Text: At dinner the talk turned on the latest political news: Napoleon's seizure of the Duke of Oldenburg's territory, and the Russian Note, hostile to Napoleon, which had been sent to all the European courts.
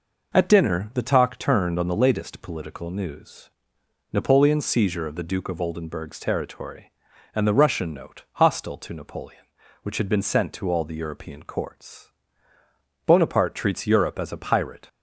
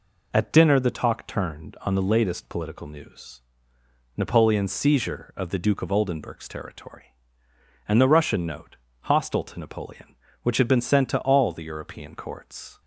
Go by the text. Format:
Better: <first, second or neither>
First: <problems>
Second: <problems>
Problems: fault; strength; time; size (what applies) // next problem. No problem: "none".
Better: second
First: goes on to say "Bonaparte treats Europe as a pirate"; strong; from 13.0 s on; 1.8 s long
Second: none